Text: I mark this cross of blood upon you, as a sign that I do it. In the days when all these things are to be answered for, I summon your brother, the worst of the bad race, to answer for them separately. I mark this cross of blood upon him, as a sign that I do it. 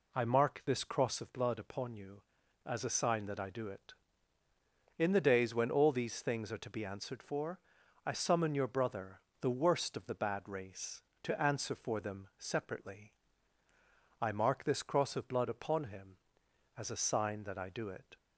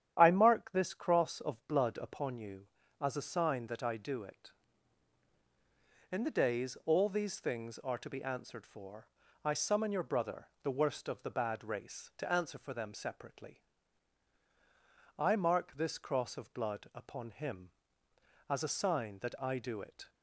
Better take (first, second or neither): first